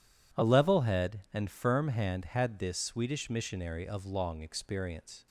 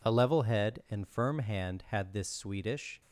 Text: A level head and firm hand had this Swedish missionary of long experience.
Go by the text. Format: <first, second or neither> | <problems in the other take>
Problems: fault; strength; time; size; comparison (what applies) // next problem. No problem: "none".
first | stops before "missionary of long experience"; at 3.0 s